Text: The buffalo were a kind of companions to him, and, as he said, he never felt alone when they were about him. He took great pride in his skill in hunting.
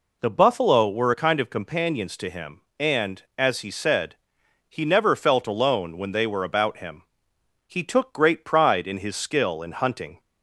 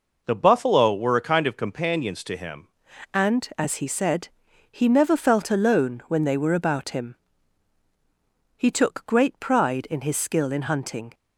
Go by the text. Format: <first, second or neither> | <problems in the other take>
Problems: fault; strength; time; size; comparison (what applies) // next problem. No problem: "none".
first | changes voice at "and"; from 3.1 s on; 8.0 s long